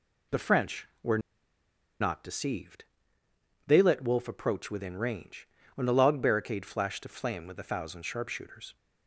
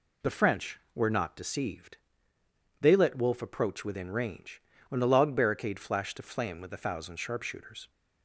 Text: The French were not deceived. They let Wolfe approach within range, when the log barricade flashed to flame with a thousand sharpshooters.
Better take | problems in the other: second | pauses between "were" and "not"; noticeable; at 1.1 s; 0.81 s long

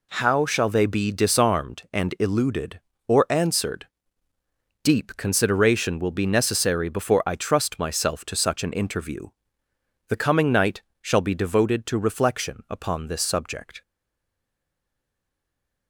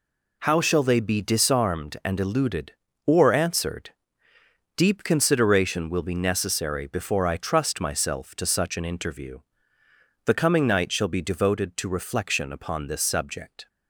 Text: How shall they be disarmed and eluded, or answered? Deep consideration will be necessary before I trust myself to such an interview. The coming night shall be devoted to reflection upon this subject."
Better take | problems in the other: second | pauses between "night" and "shall"; slight; at 10.8 s; 0.18 s long // stays silent after the last word; noticeable; from 13.8 s on; 2.0 s long

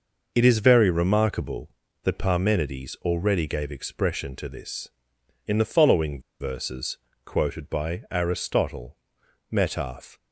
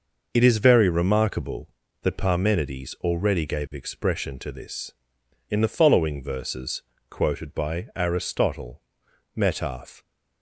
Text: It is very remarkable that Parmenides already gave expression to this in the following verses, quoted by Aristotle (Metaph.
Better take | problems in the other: second | pauses between "following" and "verses"; slight; at 6.2 s; 0.19 s long

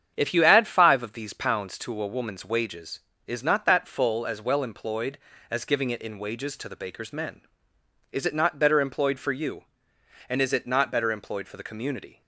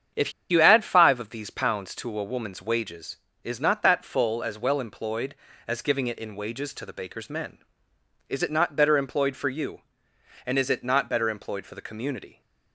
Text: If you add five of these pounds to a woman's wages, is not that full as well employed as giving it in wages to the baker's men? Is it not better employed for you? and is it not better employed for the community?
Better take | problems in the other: first | starts louder than the rest; strong; until 1.3 s; 8 dB; strong in the first // pauses between "If" and "you"; slight; at 0.3 s; 0.18 s long

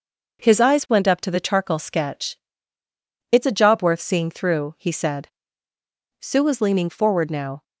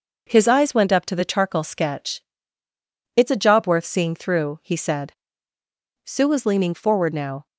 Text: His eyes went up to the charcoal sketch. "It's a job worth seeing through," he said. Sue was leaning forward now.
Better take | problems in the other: neither | none

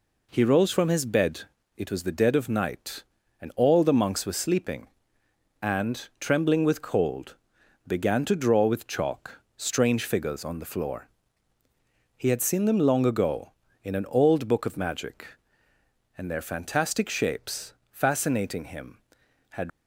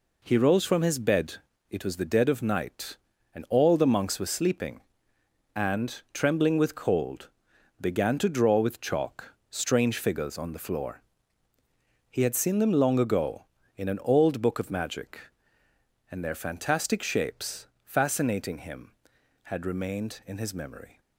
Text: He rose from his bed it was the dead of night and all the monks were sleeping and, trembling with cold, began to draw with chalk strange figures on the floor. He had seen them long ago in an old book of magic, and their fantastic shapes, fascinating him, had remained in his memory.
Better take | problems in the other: second | pauses between "bed" and "it"; slight; at 1.4 s; 0.34 s long; slight in the second // pauses between "chalk" and "strange"; slight; at 9.3 s; 0.16 s long; slight in the second // stops before "remained in his memory"; at 19.7 s

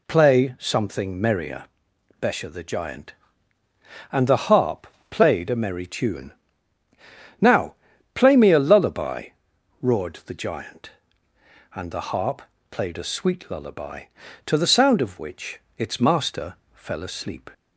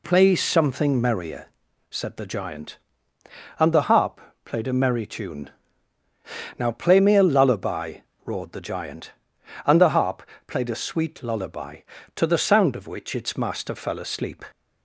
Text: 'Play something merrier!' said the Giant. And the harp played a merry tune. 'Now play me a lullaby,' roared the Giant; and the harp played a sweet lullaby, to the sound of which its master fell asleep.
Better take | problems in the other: second | says "besha" for "said"; at 2.1 s // pauses between "harp" and "played"; slight; at 4.8 s; 0.24 s long; slight in the second // pauses between "Now" and "play"; at 7.7 s; 0.40 s long // pauses between "harp" and "played"; slight; at 12.4 s; 0.28 s long; slight in the second // pauses between "which" and "its"; slight; at 15.5 s; 0.18 s long // pauses between "master" and "fell"; slight; at 16.5 s; 0.18 s long

